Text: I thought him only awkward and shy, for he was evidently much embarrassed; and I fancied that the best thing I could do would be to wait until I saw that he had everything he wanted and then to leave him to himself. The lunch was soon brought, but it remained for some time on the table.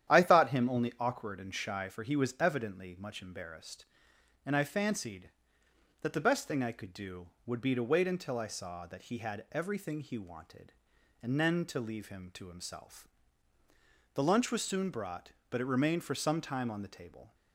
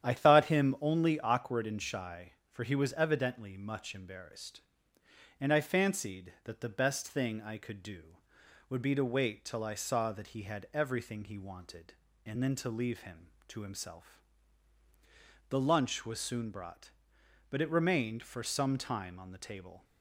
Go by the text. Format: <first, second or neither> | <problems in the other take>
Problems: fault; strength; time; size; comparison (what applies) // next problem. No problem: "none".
first | starts louder than the rest; strong; until 1.1 s; 10 dB; strong in the first // says "till" for "until"; at 9.4 s